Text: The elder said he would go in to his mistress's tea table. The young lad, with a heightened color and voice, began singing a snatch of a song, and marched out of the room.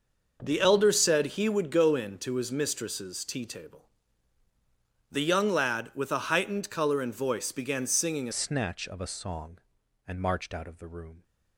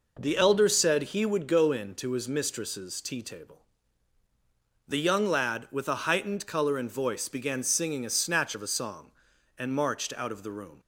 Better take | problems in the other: second | starts louder than the rest; noticeable; until 1.4 s; 6 dB // changes voice at "snatch"; from 8.3 s on; 2.9 s long

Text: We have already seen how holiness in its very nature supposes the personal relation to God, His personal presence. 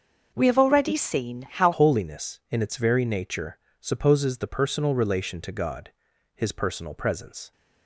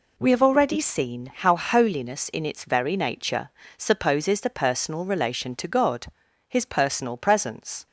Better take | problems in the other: second | starts louder than the rest; until 1.3 s; 6.5 dB // changes voice at "holiness"; from 1.7 s on; 5.8 s long // pauses between "nature" and "supposes"; slight; at 3.5 s; 0.20 s long; slight in the second

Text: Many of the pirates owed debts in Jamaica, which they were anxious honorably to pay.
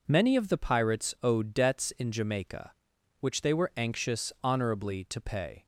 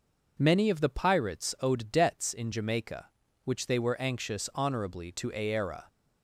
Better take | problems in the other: first | says "aera" for "pay"; at 5.3 s

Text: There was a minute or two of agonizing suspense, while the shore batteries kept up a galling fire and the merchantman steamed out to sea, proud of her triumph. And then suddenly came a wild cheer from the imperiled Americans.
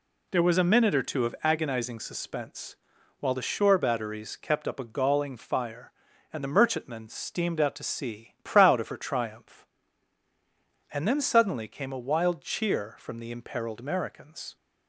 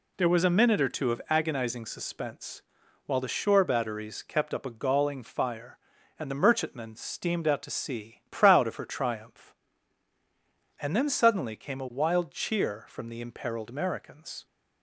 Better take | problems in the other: neither | none

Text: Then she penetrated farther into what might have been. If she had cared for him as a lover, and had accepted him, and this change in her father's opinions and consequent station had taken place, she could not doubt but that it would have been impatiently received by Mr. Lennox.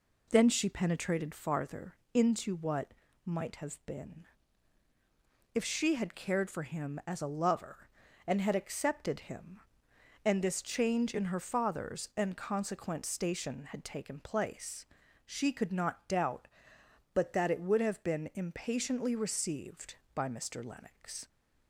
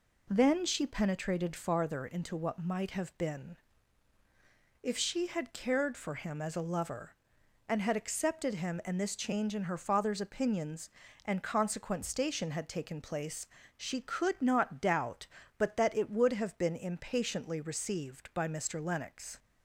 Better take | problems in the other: second | pauses between "farther" and "into"; slight; at 1.9 s; 0.18 s long // pauses between "what" and "might"; slight; at 2.9 s; 0.32 s long // skips "opinions"; at 12.1 s

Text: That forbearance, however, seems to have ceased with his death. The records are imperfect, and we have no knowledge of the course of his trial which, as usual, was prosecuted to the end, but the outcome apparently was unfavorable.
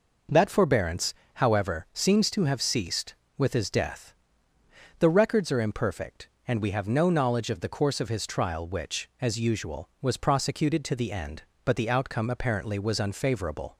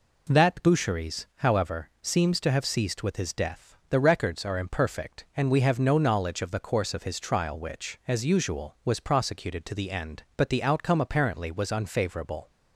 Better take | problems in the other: first | says "boucheries" for "forbearance"; at 0.6 s

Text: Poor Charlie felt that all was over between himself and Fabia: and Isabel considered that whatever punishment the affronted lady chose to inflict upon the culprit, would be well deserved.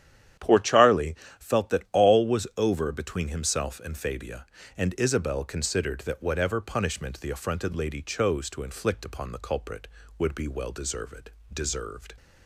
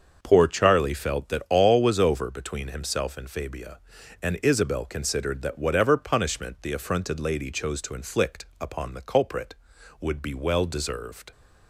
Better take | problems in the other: second | starts louder than the rest; strong; until 1.6 s; 10.5 dB; also in the second // pauses between "Charlie" and "felt"; slight; at 1.1 s; 0.23 s long // says "deserved" twice; at 11.5 s

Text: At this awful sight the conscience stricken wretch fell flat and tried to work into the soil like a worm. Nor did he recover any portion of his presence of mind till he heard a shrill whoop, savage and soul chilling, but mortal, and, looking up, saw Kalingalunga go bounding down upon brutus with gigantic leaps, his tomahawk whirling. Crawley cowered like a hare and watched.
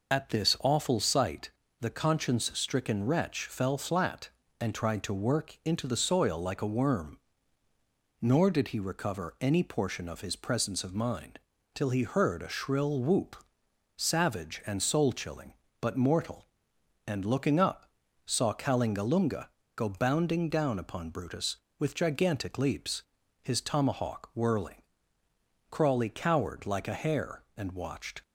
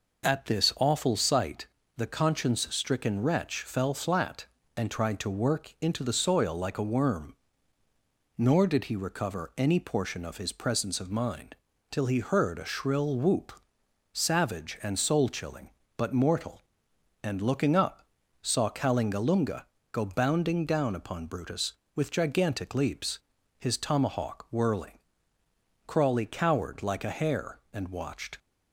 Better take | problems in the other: second | loses the start of "At"; at 0.1 s; 40 ms // pauses between "sight" and "the"; slight; at 1.4 s; 0.32 s long; slight in the second // pauses between "mind" and "till"; slight; at 11.3 s; 0.34 s long; slight in the second // pauses between "Kalingalunga" and "go"; slight; at 19.4 s; 0.26 s long; slight in the second

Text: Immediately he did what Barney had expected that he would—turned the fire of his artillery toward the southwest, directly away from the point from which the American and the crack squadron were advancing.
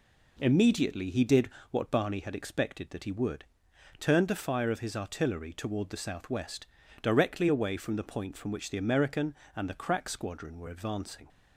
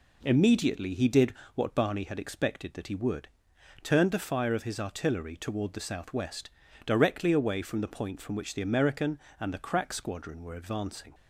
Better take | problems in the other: neither | pauses between "did" and "what"; slight; the same in both

